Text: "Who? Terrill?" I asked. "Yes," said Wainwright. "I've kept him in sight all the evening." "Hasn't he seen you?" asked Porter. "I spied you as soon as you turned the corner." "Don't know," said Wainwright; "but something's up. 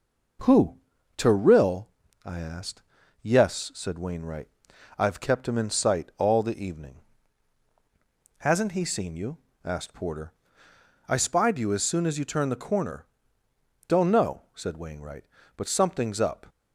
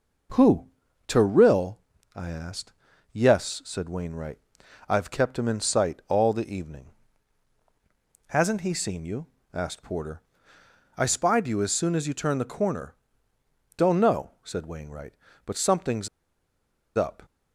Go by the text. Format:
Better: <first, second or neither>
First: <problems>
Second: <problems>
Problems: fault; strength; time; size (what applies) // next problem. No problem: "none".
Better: first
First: none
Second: pauses between "something's" and "up"; noticeable; at 16.0 s; 0.87 s long